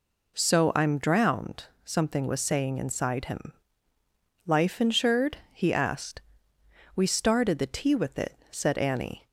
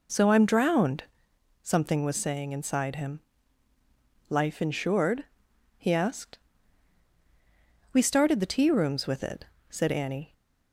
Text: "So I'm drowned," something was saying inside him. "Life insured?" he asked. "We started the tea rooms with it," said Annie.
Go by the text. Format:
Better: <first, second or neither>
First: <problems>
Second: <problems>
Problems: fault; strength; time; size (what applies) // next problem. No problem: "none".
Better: second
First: skips "rooms"; at 7.9 s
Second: none